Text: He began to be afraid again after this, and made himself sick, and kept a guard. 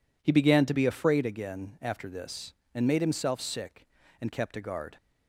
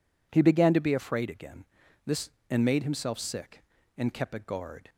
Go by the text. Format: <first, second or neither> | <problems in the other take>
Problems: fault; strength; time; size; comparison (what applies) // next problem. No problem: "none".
first | skips "after"; at 1.8 s